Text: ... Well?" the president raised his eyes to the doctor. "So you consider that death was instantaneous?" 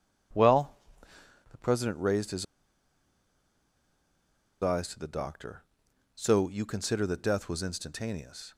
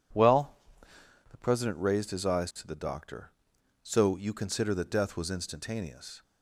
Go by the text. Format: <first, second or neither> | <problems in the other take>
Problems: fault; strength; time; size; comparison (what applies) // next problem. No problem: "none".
second | pauses between "his" and "eyes"; strong; at 2.4 s; 2.1 s long